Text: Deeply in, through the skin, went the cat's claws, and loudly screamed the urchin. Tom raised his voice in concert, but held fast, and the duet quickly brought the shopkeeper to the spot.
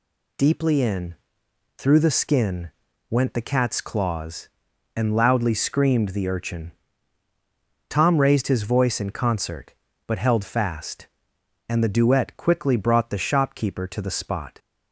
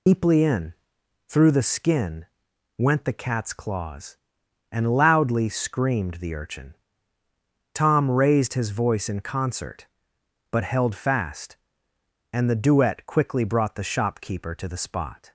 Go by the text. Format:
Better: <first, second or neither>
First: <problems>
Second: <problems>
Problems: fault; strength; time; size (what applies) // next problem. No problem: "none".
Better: first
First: none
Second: loses the start of "Deeply"; at 0.0 s; 100 ms